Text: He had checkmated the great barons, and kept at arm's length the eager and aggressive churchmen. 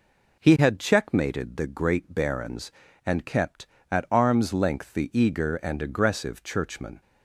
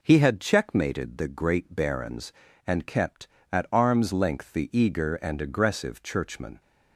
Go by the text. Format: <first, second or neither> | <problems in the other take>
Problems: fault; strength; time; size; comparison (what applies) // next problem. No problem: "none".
neither | none